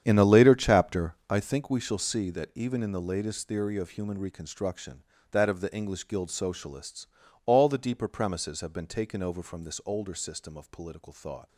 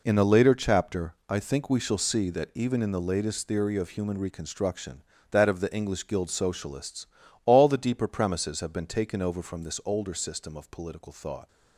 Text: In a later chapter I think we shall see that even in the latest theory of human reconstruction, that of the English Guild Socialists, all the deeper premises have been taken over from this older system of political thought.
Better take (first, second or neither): second